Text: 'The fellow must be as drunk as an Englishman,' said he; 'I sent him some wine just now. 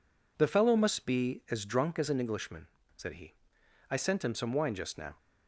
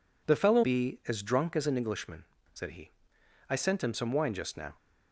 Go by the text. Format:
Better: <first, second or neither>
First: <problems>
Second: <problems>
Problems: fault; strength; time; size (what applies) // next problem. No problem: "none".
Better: first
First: none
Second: skips "must"; at 0.6 s